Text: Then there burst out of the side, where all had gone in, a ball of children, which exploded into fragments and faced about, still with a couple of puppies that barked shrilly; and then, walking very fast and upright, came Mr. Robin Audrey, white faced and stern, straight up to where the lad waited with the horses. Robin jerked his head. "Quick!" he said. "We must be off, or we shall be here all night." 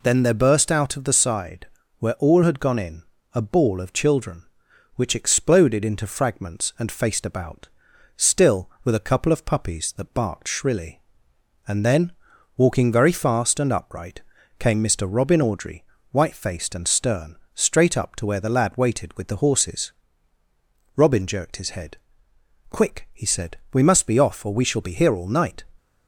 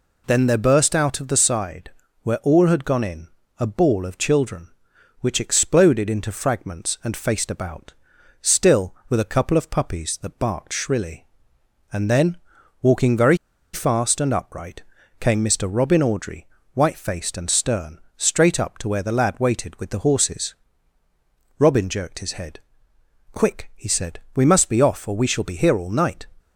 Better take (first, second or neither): first